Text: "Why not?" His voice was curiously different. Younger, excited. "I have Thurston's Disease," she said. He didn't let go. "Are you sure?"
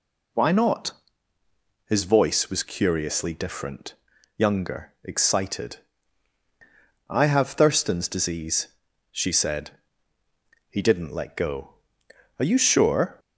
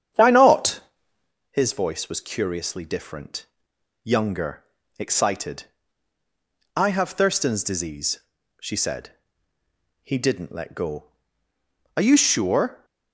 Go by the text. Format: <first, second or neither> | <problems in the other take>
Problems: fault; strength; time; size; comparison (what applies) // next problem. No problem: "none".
first | starts louder than the rest; strong; until 1.3 s; 9 dB